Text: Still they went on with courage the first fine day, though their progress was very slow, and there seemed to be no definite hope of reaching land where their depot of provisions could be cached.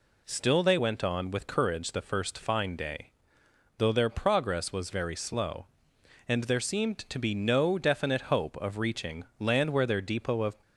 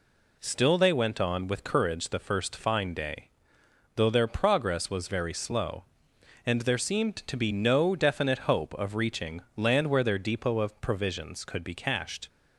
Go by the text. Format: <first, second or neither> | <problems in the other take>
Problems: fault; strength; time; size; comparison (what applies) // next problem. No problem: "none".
second | stops before "provisions could be cached"; at 10.6 s